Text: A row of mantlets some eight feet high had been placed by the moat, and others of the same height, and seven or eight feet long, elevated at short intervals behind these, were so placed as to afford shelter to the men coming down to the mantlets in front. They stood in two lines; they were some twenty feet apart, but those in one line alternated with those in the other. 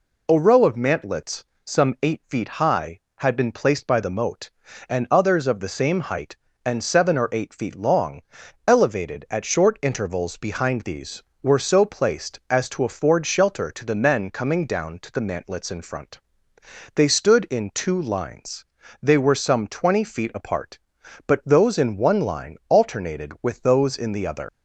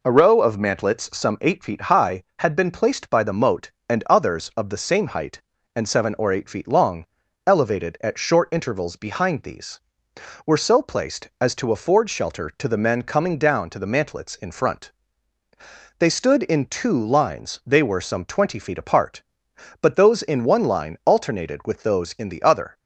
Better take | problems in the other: second | pauses between "mantlets" and "some"; slight; at 1.4 s; 0.22 s long // leaves "other" unfinished; at 24.4 s; 70 ms

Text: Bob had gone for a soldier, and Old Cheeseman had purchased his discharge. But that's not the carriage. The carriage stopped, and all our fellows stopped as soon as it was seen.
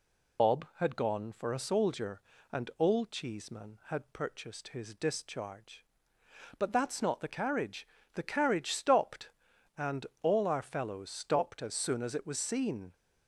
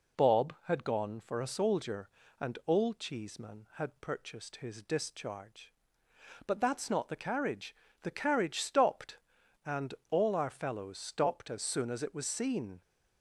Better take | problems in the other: second | loses the start of "Bob"; at 0.3 s; 110 ms // pauses between "and" and "all"; slight; at 10.0 s; 0.16 s long; slight in the second

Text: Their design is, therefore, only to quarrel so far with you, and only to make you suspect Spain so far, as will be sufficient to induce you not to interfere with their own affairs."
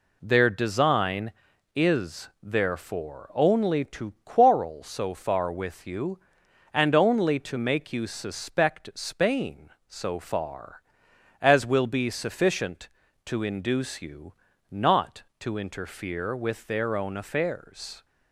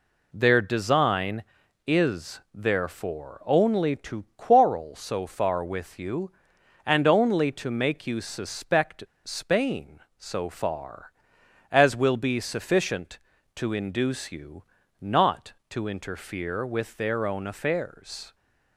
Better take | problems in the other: first | pauses between "suspect" and "Spain"; slight; at 9.0 s; 0.22 s long // pauses between "you" and "not"; at 14.6 s; 0.38 s long; also in the first

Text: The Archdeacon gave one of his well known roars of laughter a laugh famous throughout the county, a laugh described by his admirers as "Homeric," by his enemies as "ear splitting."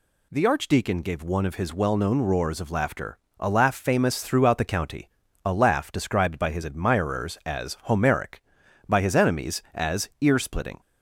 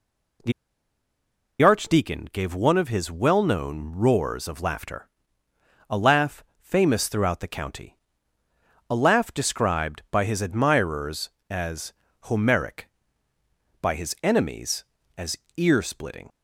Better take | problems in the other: first | pauses between "The" and "Archdeacon"; at 0.5 s; 1.1 s long // pauses between "laughter" and "a"; noticeable; at 5.0 s; 0.80 s long; slight in the first // pauses between "laugh" and "famous"; slight; at 6.4 s; 0.16 s long // pauses between "as" and "Homeric"; slight; at 11.9 s; 0.30 s long // pauses between "as" and "ear"; slight; at 15.3 s; 0.18 s long

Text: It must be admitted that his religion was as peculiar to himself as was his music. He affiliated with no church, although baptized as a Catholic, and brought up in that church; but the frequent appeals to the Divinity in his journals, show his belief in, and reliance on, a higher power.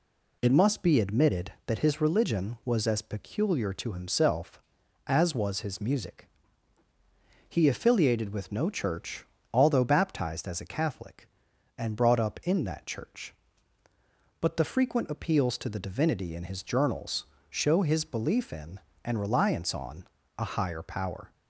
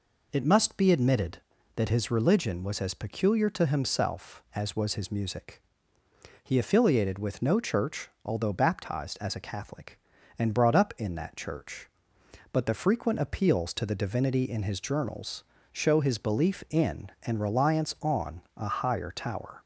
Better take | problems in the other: first | says "tower" for "power"; at 19.1 s

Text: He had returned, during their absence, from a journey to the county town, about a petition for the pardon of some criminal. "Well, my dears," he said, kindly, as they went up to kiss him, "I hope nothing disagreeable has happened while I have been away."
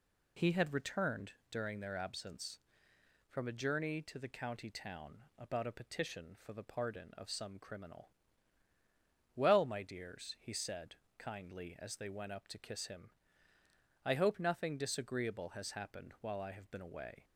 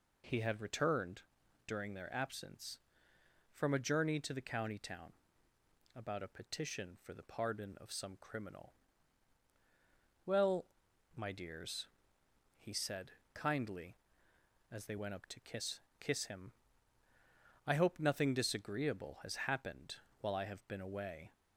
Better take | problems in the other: first | says "kiss" twice; at 15.9 s // pauses between "happened" and "while"; slight; at 19.9 s; 0.24 s long

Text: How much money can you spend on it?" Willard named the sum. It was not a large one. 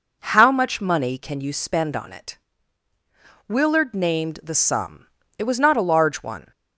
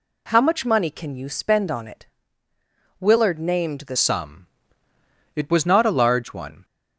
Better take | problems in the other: first | changes voice at "sum"; from 3.9 s on; 2.7 s long

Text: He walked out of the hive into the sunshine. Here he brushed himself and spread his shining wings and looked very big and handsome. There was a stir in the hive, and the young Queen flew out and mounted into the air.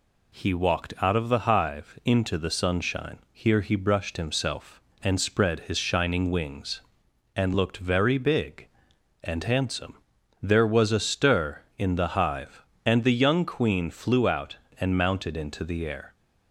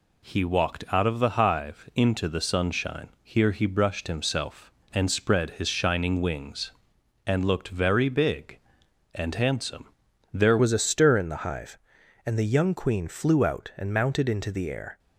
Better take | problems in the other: first | changes voice at "was"; from 10.5 s on; 4.4 s long

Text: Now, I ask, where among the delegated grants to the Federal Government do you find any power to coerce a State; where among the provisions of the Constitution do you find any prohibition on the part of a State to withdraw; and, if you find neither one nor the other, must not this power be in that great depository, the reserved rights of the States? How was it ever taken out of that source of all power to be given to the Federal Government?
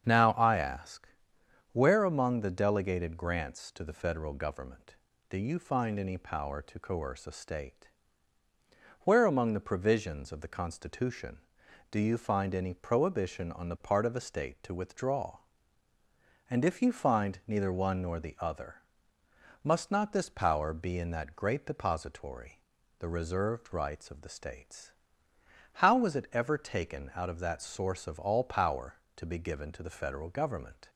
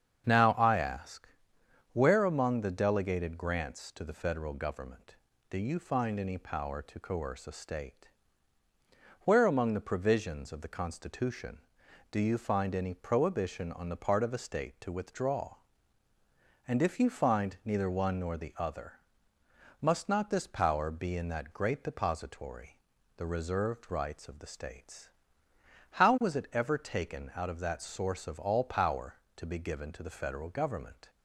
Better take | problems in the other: neither | starts louder than the rest; strong; the same in both

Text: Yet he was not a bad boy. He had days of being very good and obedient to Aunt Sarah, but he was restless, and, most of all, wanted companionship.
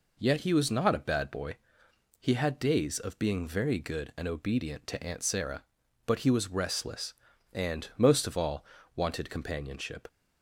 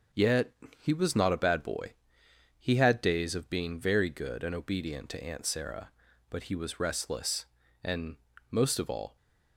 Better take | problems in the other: first | starts louder than the rest; until 1.4 s; 6 dB // pauses between "Yet" and "he"; slight; at 0.5 s; 0.26 s long // stops before "wanted companionship"; at 9.1 s

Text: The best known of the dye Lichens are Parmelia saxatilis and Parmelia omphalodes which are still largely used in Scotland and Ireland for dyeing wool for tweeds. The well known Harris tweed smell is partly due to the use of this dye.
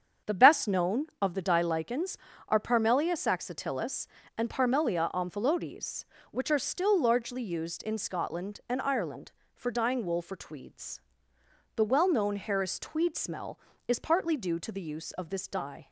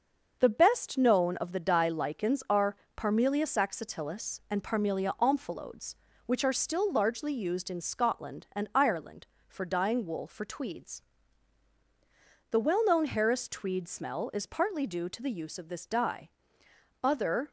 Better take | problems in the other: first | starts louder than the rest; until 1.4 s; 6.5 dB; strong in the first // pauses between "are" and "Parmelia"; slight; at 2.7 s; 0.20 s long // goes on to say "Other"; slight; from 17.0 s on; 0.48 s long

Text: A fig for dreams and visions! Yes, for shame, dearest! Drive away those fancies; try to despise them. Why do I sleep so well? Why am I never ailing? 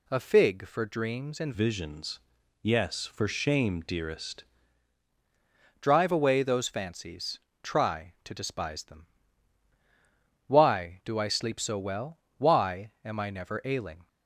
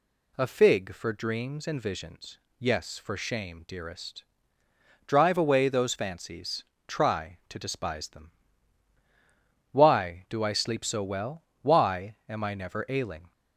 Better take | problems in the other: second | changes voice from "visions" to "dearest"; from 1.5 to 4.4 s; 2.9 s long

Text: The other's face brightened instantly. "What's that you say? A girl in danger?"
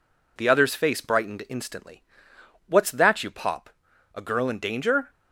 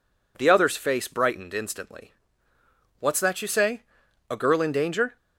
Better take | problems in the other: second | says "pop" for "say"; at 3.2 s

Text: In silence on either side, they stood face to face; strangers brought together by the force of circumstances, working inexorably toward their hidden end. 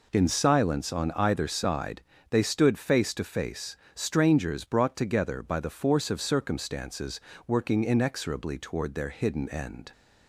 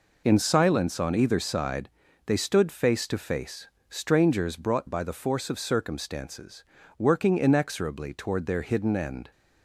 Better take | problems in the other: first | skips "together"; at 4.8 s

